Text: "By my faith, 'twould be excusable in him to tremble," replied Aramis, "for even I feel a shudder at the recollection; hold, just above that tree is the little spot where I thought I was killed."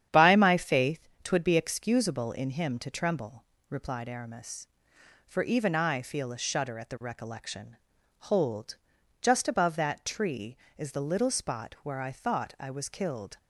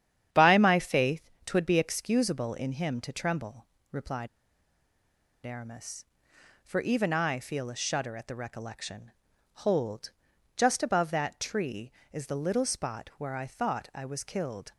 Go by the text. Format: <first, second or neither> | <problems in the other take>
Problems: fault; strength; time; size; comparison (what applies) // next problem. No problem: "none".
first | starts louder than the rest; strong; until 1.4 s; 9.5 dB; strong in the first // pauses between "replied" and "Aramis"; at 4.2 s; 1.1 s long